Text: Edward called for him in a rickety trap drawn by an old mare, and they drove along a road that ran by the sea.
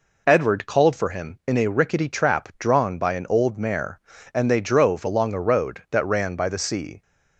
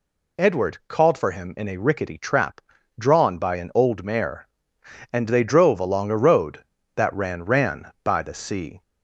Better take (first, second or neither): first